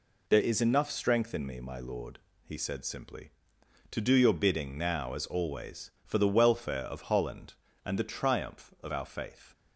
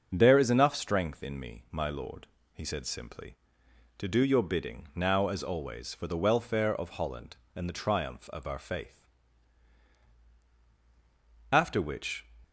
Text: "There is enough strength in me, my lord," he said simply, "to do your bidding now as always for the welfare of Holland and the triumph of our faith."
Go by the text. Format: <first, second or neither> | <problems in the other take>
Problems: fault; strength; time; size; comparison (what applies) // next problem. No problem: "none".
first | starts louder than the rest; until 1.1 s; 6 dB // goes on to say "After which"; noticeable; from 11.5 s on; 0.72 s long